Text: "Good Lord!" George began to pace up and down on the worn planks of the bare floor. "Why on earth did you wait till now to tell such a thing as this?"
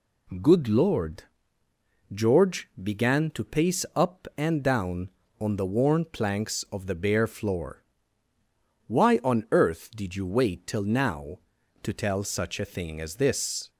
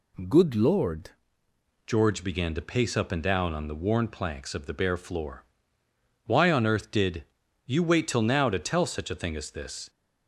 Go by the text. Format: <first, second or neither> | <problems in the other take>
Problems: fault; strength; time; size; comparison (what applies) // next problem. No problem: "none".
first | changes voice at "George"; from 1.8 s on; 8.0 s long // pauses between "did" and "you"; at 7.2 s; 0.42 s long